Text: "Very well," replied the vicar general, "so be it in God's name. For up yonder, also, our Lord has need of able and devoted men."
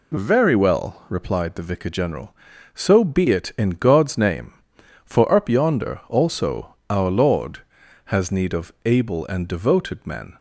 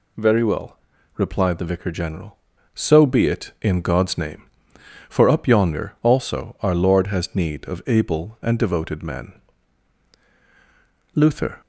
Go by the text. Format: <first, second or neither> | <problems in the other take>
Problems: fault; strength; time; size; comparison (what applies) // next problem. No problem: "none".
first | goes on to say "Luther"; slight; from 11.1 s on; 0.46 s long